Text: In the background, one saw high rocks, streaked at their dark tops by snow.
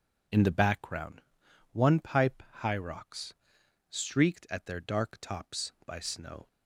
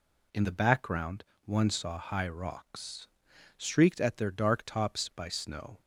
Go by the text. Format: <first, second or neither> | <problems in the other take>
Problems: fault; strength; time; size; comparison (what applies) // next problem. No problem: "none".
second | says "pipe" for "saw"; at 1.9 s